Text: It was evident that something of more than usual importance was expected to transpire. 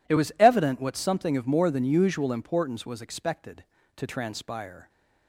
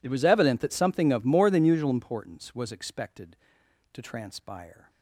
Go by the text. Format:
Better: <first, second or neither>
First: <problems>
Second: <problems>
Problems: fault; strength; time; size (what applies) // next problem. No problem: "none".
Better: second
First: says "what" for "that"; at 0.8 s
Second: none